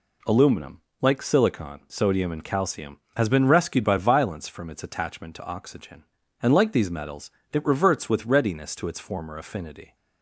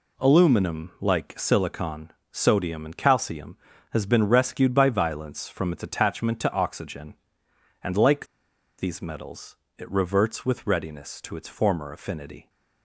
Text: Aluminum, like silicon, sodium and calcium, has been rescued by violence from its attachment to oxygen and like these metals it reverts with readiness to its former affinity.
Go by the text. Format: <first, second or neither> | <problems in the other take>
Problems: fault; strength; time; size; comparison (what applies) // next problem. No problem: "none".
first | pauses between "like" and "these"; noticeable; at 8.2 s; 0.52 s long // pauses between "metals" and "it"; slight; at 9.5 s; 0.24 s long; slight in the first